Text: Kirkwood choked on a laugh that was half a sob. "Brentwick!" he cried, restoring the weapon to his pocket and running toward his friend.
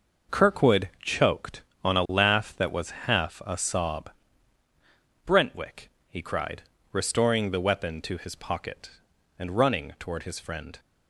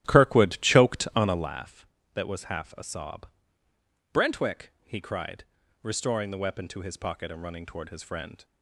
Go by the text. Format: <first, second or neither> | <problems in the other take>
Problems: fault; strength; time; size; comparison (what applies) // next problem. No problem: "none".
first | starts louder than the rest; strong; until 1.6 s; 13.5 dB